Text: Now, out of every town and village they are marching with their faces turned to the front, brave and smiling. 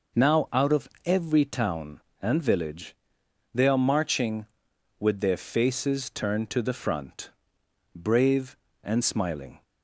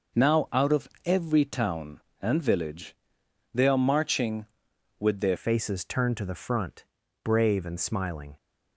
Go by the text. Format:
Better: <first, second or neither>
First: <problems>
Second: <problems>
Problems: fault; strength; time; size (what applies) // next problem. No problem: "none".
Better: first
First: pauses between "of" and "every"; slight; at 0.8 s; 0.16 s long // pauses between "village" and "they"; noticeable; at 2.9 s; 0.60 s long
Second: pauses between "of" and "every"; slight; at 0.8 s; 0.16 s long // pauses between "village" and "they"; noticeable; at 2.9 s; 0.60 s long // changes voice at "faces"; from 5.3 s on; 3.0 s long